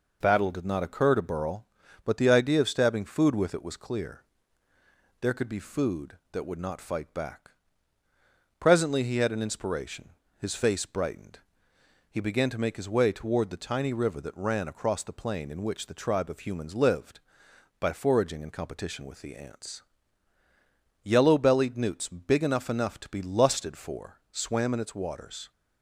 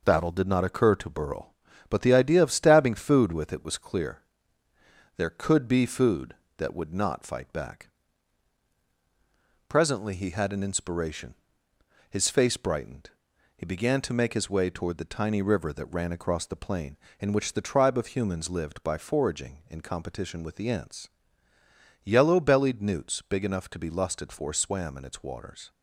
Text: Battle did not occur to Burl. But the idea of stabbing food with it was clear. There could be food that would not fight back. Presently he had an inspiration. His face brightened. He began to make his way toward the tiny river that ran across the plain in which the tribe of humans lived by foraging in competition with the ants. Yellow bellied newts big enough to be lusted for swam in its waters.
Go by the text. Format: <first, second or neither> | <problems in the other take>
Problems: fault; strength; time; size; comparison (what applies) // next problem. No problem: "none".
second | says "enough" twice; at 22.6 s